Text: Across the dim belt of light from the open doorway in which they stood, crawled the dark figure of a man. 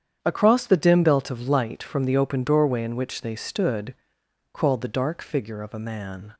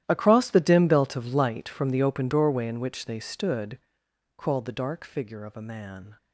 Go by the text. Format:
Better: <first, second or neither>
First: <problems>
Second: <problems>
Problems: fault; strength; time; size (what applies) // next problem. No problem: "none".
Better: first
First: starts louder than the rest; strong; until 1.2 s; 8.5 dB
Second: gets quieter; strong; throughout; 17 dB // starts louder than the rest; strong; until 1.0 s; 12.5 dB